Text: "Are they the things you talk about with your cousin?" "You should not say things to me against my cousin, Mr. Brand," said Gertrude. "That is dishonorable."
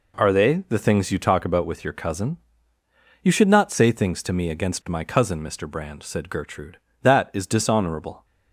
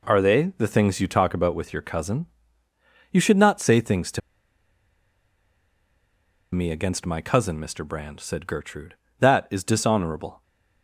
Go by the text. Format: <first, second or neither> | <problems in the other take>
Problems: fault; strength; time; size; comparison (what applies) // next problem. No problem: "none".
first | pauses between "to" and "me"; strong; at 4.2 s; 2.3 s long